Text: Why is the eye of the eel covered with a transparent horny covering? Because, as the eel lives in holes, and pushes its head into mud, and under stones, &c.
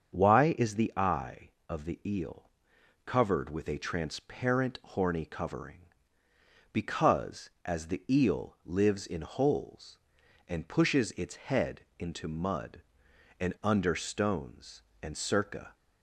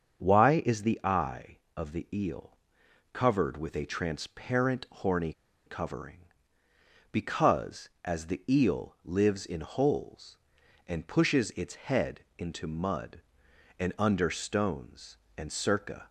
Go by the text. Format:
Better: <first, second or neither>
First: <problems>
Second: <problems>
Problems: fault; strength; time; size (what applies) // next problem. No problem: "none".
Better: first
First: starts louder than the rest; strong; until 1.2 s; 7 dB // pauses between "eel" and "covered"; noticeable; at 2.4 s; 0.56 s long // pauses between "its" and "head"; slight; at 11.3 s; 0.16 s long // pauses between "head" and "into"; slight; at 11.8 s; 0.16 s long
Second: starts louder than the rest; strong; until 1.3 s; 7 dB // pauses between "eel" and "covered"; noticeable; at 2.5 s; 0.56 s long // pauses between "horny" and "covering"; slight; at 5.3 s; 0.33 s long // pauses between "its" and "head"; slight; at 11.7 s; 0.16 s long // pauses between "head" and "into"; slight; at 12.2 s; 0.16 s long